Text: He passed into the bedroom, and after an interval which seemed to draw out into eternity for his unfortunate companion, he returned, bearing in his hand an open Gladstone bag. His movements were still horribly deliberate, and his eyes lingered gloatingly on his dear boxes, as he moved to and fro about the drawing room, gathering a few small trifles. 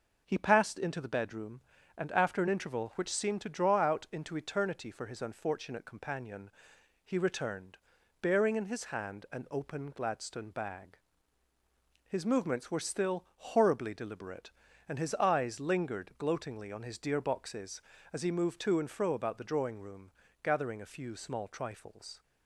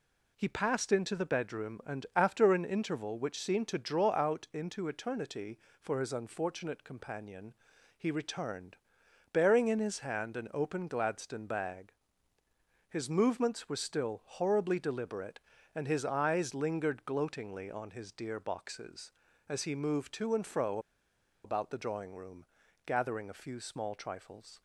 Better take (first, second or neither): first